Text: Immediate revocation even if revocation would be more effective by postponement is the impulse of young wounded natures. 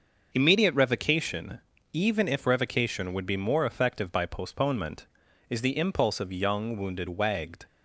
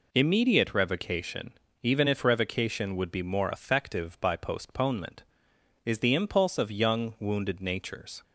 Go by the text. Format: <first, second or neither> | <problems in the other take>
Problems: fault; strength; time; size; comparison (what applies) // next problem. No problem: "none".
second | starts louder than the rest; until 1.3 s; 6.5 dB // pauses between "revocation" and "even"; slight; at 1.5 s; 0.34 s long; slight in the second // says "wagged" for "natures"; at 7.0 s